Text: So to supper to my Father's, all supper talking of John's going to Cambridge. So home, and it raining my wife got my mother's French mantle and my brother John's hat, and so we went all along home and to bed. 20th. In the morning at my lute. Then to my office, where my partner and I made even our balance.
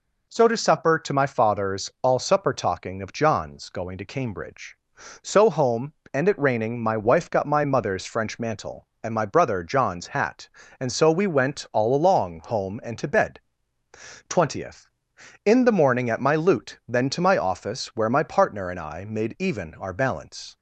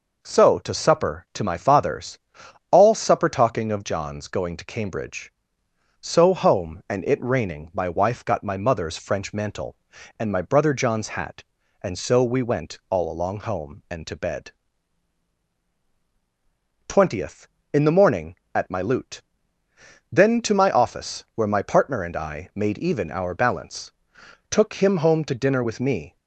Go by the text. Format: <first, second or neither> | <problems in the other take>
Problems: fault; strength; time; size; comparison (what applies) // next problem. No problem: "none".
first | goes on to say "Took him home to dinner with me"; strong; from 24.4 s on; 1.6 s long